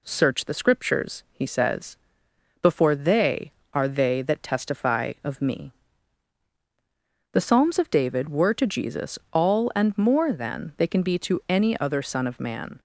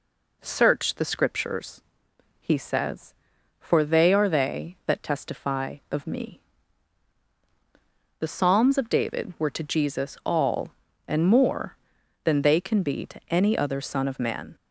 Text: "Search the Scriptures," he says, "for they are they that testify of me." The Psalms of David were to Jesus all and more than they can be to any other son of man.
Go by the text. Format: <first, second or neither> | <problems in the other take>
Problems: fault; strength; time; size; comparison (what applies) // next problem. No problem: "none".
second | says "before" for "for"; at 2.6 s